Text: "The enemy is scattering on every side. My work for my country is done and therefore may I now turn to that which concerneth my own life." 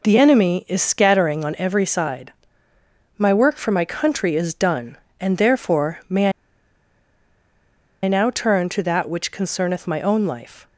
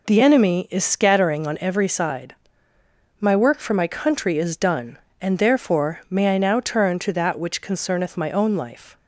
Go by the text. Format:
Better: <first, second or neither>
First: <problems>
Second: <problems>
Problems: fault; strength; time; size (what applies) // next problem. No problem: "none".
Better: second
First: pauses between "may" and "I"; strong; at 6.3 s; 1.7 s long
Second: none